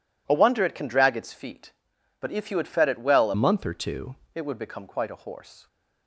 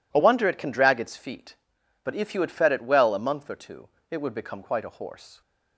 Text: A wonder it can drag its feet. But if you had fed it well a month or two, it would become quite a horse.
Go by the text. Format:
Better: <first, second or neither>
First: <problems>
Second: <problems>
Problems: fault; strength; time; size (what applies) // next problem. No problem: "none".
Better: second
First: changes voice from "month" to "two"; from 3.3 to 4.1 s; 0.8 s long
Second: none